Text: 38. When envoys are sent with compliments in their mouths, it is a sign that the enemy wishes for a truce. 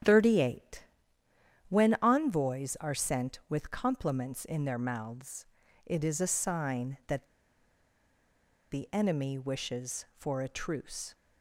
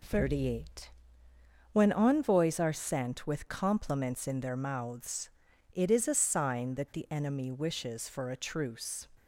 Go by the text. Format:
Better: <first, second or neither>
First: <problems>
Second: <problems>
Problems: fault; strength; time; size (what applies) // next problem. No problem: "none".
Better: second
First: starts louder than the rest; strong; until 1.9 s; 9 dB // pauses between "that" and "the"; strong; at 7.2 s; 1.4 s long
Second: none